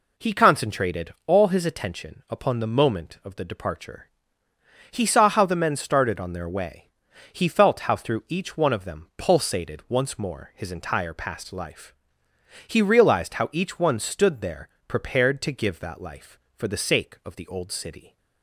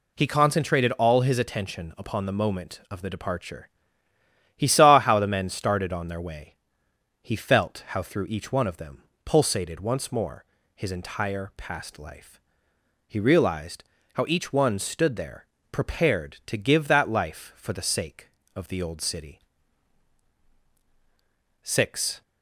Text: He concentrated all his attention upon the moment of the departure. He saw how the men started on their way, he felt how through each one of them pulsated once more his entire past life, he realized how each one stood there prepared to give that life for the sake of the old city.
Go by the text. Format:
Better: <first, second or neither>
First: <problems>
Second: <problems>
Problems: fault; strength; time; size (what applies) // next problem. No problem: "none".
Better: first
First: pauses between "there" and "prepared"; slight; at 14.6 s; 0.18 s long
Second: pauses between "them" and "pulsated"; slight; at 9.0 s; 0.20 s long // pauses between "more" and "his"; slight; at 10.4 s; 0.32 s long // pauses between "realized" and "how"; slight; at 13.8 s; 0.30 s long // pauses between "there" and "prepared"; slight; at 15.4 s; 0.26 s long // goes on to say "Six"; from 21.6 s on; 0.58 s long